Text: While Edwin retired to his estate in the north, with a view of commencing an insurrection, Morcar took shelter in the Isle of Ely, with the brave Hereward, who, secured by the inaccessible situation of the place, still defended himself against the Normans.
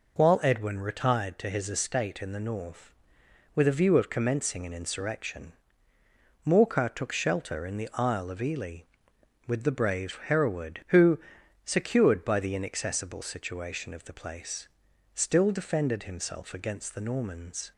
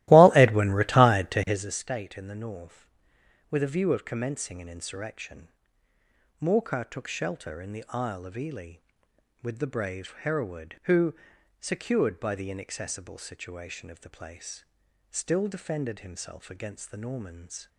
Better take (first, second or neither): first